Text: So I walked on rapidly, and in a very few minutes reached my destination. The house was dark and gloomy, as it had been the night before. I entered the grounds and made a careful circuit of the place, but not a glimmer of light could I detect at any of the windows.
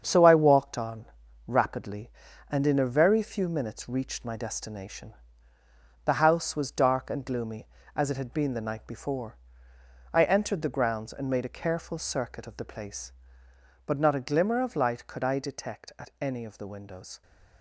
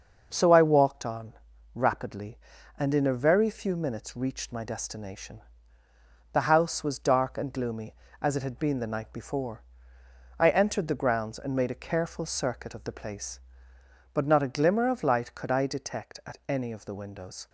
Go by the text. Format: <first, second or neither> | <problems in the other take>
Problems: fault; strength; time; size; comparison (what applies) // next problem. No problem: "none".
second | gets quieter; strong; throughout; 7.5 dB // starts louder than the rest; strong; until 1.0 s; 7.5 dB; noticeable in the second // pauses between "on" and "rapidly"; at 1.0 s; 0.42 s long; also in the second